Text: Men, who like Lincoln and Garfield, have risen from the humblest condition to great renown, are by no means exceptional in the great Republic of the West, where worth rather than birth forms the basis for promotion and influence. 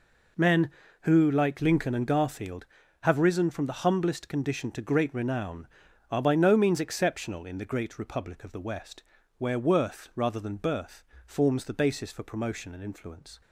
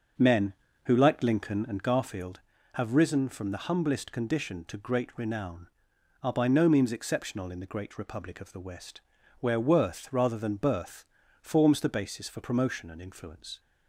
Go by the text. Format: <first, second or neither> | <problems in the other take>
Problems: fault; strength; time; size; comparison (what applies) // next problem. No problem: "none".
first | starts louder than the rest; noticeable; until 2.0 s; 6 dB // pauses between "birth" and "forms"; at 11.0 s; 0.38 s long; slight in the first